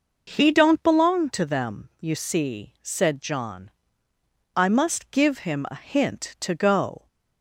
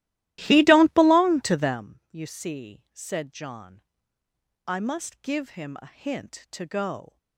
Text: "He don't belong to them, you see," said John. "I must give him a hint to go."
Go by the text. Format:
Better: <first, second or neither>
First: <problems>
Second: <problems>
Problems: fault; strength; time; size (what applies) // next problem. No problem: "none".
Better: first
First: none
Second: starts louder than the rest; strong; until 1.8 s; 15.5 dB